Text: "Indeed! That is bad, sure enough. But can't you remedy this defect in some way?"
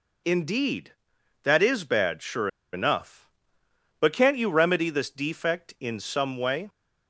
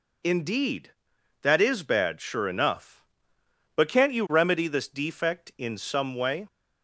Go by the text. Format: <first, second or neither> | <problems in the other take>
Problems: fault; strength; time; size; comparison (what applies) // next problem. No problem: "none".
second | pauses between "sure" and "enough"; slight; at 2.4 s; 0.25 s long